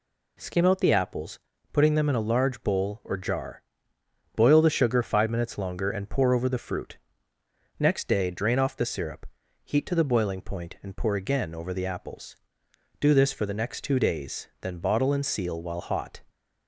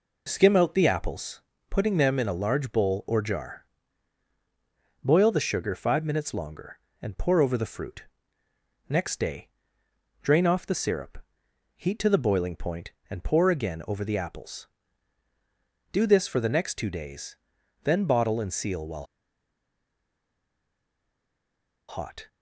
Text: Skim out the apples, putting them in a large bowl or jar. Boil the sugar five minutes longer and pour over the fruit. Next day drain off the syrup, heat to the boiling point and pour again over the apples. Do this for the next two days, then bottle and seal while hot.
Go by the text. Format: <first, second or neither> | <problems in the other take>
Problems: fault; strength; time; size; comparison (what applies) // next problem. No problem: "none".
first | pauses between "day" and "drain"; noticeable; at 9.4 s; 0.74 s long // pauses between "while" and "hot"; strong; at 19.0 s; 2.8 s long